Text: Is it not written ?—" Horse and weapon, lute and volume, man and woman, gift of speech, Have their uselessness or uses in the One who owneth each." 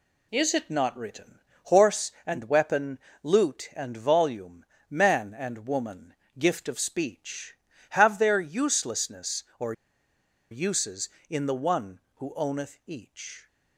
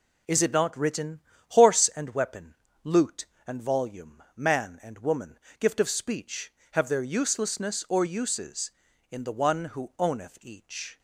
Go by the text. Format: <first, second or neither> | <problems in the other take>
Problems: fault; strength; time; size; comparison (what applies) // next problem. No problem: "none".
second | pauses between "or" and "uses"; noticeable; at 9.7 s; 0.78 s long